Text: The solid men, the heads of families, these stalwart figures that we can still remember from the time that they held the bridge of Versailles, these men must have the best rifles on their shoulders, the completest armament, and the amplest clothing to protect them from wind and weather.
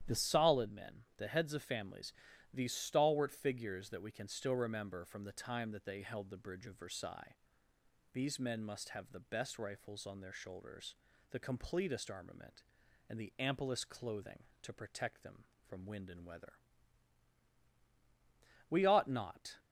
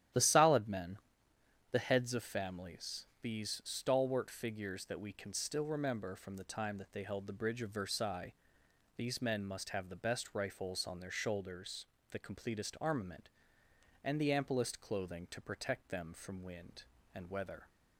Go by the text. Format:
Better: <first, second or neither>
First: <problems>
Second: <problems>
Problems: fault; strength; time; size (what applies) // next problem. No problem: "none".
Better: second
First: starts louder than the rest; strong; until 1.2 s; 11 dB // goes on to say "We ought not"; noticeable; from 18.6 s on; 0.86 s long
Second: starts louder than the rest; strong; until 1.8 s; 11.5 dB